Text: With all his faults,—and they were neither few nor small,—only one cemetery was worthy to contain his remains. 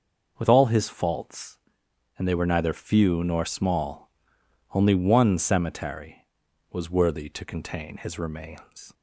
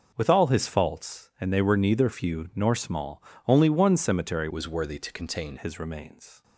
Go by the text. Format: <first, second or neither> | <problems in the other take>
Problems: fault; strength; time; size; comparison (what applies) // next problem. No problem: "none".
first | changes voice from "was" to "contain"; from 4.5 to 5.5 s; 1.0 s long